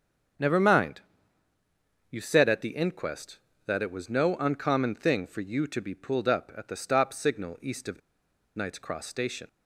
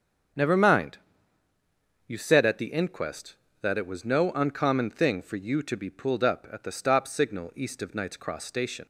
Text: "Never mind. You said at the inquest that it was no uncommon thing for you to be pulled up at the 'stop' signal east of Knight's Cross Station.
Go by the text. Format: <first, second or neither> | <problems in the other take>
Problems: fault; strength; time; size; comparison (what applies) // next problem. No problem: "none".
second | starts louder than the rest; strong; until 2.4 s; 7.5 dB; strong in the second // pauses between "of" and "Knight's"; noticeable; at 8.0 s; 0.57 s long